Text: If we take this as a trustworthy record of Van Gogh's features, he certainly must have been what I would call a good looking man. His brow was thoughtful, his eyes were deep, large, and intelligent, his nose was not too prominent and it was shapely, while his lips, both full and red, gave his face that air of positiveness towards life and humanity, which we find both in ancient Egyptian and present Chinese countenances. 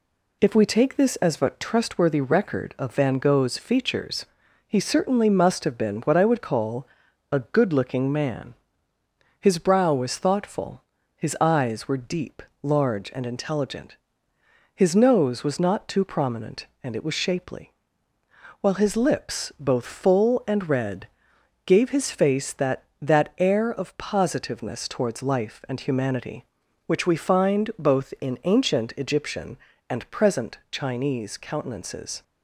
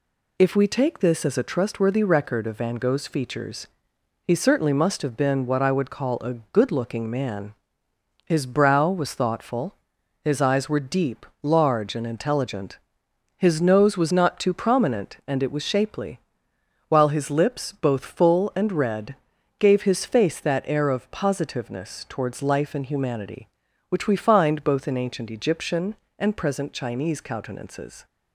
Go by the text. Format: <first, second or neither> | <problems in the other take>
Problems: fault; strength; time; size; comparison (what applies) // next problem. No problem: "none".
second | pauses between "call" and "a"; noticeable; at 6.8 s; 0.46 s long // says "that" twice; at 23.0 s